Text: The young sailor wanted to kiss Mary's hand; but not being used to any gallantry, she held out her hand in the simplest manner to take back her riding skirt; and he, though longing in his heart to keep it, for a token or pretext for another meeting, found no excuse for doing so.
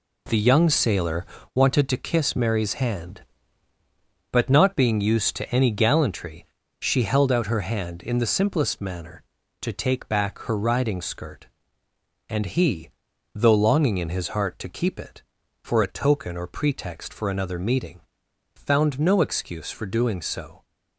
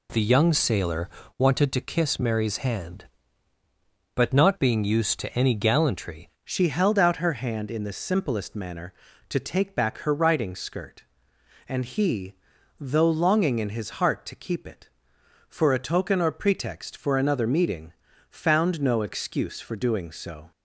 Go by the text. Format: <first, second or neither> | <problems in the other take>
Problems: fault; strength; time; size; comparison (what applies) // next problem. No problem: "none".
first | pauses between "sailor" and "wanted"; slight; at 1.0 s; 0.30 s long; slight in the first // changes voice at "she"; from 6.4 s on; 14.1 s long